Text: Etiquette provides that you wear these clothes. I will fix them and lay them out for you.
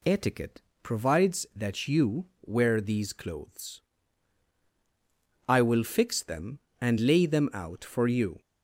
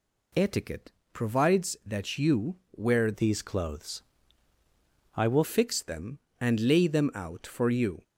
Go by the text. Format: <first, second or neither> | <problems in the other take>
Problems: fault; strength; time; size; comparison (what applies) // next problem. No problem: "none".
first | pauses between "Etiquette" and "provides"; slight; at 0.8 s; 0.22 s long; slight in the first // pauses between "you" and "wear"; slight; at 2.5 s; 0.20 s long; slight in the first // changes voice from "these" to "will"; from 3.1 to 5.4 s; 2.3 s long